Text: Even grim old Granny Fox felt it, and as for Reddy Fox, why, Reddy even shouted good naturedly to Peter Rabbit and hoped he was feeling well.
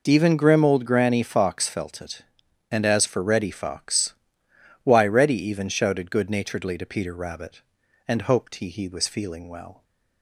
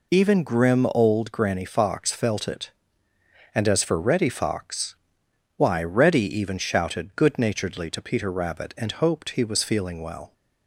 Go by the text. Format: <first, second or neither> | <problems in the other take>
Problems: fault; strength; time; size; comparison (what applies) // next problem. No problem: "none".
second | says "he" twice; at 8.6 s